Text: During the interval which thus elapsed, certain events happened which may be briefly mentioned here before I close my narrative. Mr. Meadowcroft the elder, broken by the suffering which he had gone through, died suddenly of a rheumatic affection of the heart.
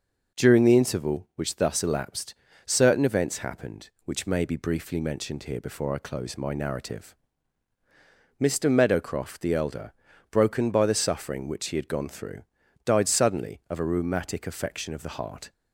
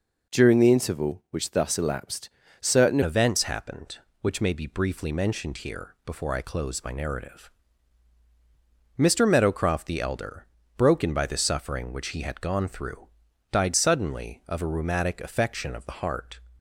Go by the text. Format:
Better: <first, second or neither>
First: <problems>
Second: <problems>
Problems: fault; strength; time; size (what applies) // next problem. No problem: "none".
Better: first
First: none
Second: changes voice at "events"; from 3.0 s on; 13.3 s long